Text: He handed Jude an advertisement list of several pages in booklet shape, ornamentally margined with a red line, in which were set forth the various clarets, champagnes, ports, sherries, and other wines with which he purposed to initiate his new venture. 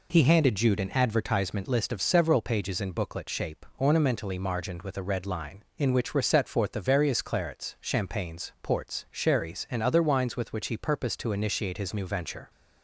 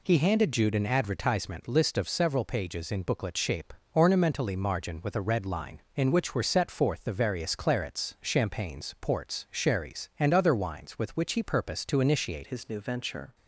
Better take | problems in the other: first | changes voice at "his"; from 12.4 s on; 0.9 s long

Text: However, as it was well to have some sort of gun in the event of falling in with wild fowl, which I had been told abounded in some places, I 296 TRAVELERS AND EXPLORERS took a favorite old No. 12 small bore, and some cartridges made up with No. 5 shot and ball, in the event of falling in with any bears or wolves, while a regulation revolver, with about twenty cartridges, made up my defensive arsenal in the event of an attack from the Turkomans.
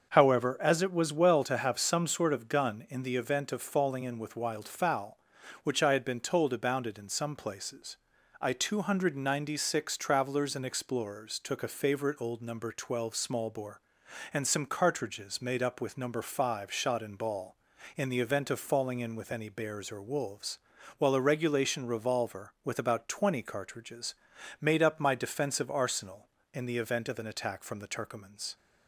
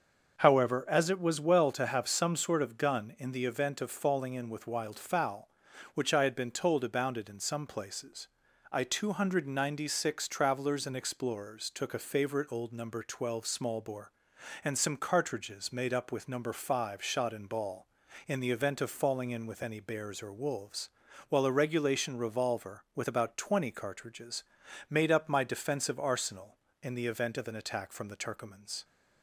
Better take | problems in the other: neither | starts louder than the rest; the same in both

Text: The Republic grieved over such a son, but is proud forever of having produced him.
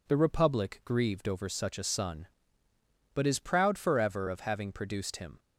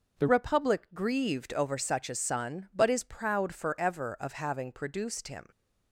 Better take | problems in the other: first | changes voice at "Republic"; from 0.2 s on; 5.2 s long

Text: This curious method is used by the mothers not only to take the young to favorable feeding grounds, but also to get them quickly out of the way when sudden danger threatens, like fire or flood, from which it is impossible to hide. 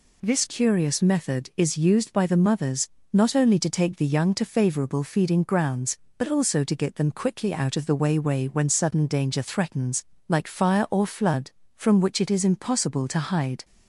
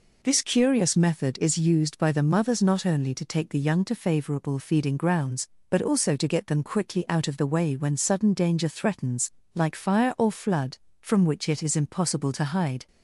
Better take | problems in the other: second | pauses between "mothers" and "not"; slight; at 2.8 s; 0.24 s long // says "way" twice; at 8.1 s

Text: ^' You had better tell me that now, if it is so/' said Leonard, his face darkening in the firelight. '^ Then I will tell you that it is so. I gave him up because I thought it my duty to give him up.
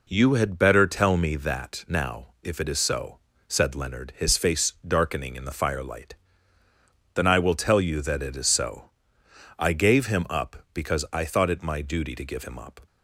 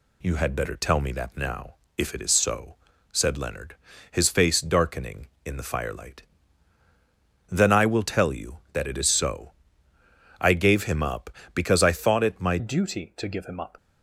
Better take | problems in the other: first | changes voice at "duty"; from 12.5 s on; 1.2 s long

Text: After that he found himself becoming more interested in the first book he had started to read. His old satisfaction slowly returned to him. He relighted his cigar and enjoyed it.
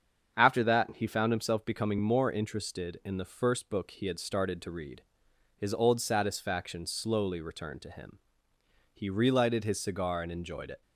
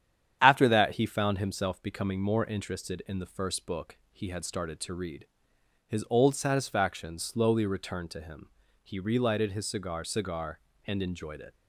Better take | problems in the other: first | starts louder than the rest; strong; until 1.4 s; 9.5 dB; strong in the first // says "cigar" twice; at 10.0 s

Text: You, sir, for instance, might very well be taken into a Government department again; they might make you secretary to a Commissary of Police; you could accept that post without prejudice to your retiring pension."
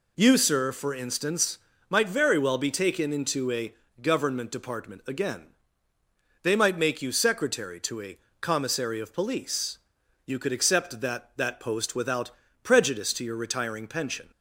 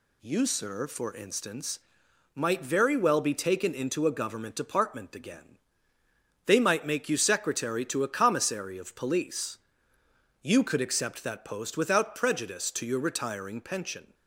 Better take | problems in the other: second | pauses between "a" and "Government"; slight; at 3.7 s; 0.30 s long // pauses between "a" and "Commissary"; slight; at 8.1 s; 0.22 s long // says "that" twice; at 11.3 s // pauses between "without" and "prejudice"; slight; at 12.3 s; 0.34 s long

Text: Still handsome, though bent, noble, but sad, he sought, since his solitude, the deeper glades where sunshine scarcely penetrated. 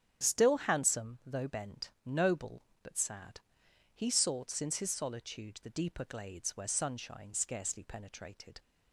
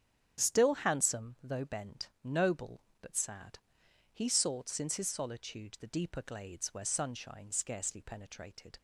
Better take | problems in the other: neither | starts louder than the rest; strong; the same in both

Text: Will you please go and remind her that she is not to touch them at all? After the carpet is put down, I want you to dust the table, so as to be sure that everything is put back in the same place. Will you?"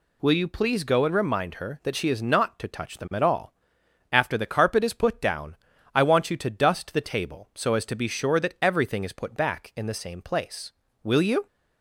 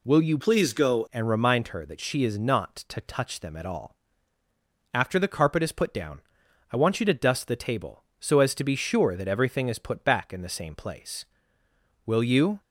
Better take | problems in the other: first | changes voice from "please" to "go"; from 0.3 to 1.0 s; 0.7 s long

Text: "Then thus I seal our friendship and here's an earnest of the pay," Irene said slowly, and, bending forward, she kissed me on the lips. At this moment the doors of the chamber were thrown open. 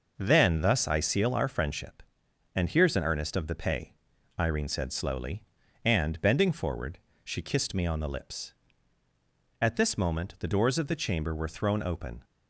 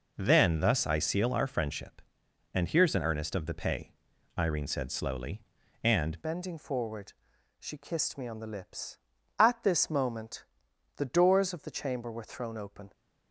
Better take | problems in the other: first | changes voice at "bending"; from 6.2 s on; 6.7 s long // pauses between "moment" and "the"; noticeable; at 10.4 s; 0.54 s long

